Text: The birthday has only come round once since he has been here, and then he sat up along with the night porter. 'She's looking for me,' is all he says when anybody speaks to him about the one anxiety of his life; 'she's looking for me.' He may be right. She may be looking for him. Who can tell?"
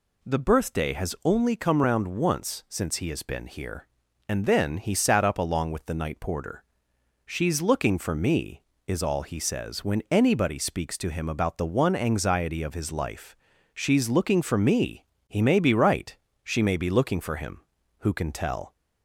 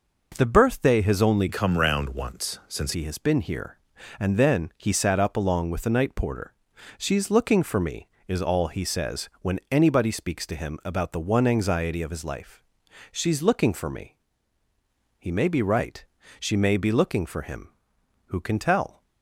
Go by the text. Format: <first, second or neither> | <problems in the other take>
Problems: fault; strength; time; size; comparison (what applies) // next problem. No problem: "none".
first | changes voice from "come" to "since"; from 1.4 to 2.9 s; 1.5 s long